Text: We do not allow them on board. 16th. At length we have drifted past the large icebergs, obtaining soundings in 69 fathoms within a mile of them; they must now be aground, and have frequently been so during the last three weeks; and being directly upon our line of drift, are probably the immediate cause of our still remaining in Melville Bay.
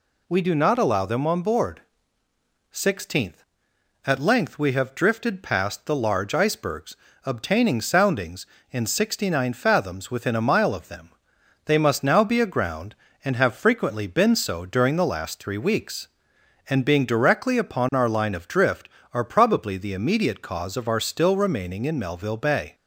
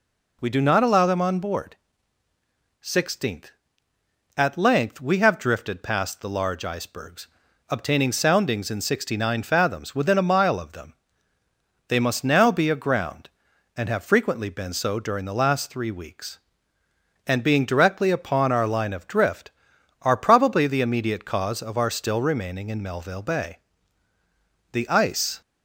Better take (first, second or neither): first